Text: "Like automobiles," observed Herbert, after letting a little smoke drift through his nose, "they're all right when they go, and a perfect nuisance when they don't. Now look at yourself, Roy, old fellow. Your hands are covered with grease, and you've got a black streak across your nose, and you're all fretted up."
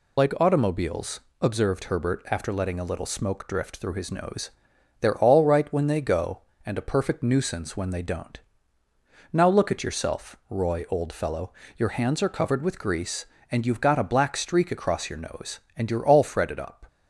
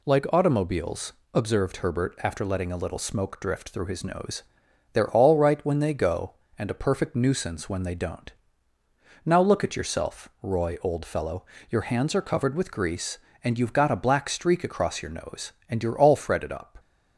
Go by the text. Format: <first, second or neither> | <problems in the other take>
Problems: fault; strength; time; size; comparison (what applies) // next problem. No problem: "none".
second | loses the start of "Like"; at 0.1 s; 65 ms